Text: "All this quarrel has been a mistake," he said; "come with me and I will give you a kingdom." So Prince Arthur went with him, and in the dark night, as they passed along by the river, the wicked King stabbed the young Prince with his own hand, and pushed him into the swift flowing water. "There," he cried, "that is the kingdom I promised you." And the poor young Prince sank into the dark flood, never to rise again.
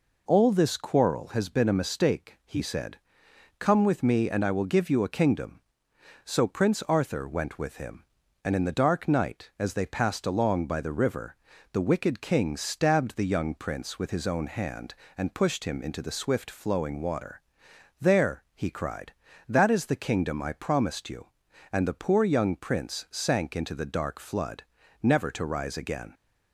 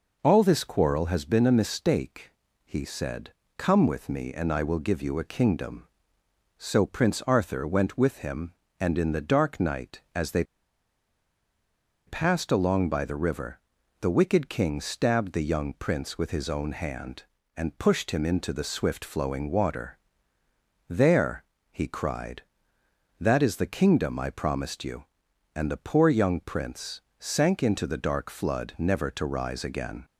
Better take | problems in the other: first | pauses between "they" and "passed"; strong; at 10.4 s; 1.6 s long // pauses between "Prince" and "sank"; slight; at 27.0 s; 0.18 s long

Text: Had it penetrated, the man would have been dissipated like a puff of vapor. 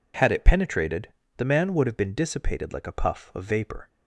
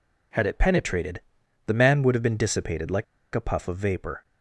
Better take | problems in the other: first | pauses between "like" and "a"; slight; at 3.0 s; 0.28 s long

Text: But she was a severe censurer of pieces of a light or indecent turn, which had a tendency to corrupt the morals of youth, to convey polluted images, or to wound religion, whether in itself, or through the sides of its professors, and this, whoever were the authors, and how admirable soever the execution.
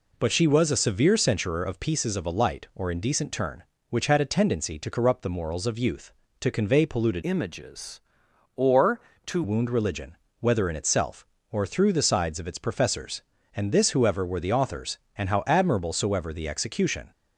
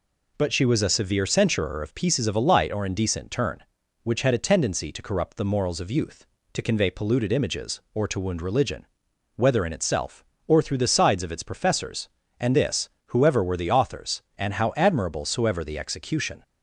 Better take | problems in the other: second | changes voice from "images" to "to"; from 7.2 to 9.4 s; 2.2 s long

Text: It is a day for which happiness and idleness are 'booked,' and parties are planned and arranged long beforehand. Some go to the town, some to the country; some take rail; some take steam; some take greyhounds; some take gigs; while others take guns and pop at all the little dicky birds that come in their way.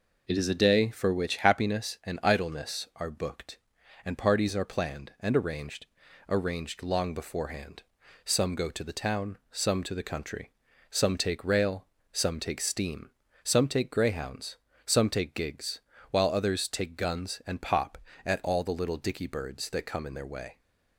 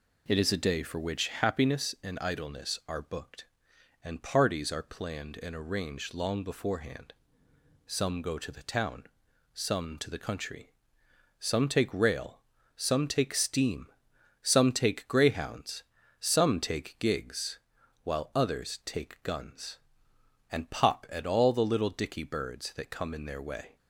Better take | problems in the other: second | says "arranged" twice; at 6.2 s

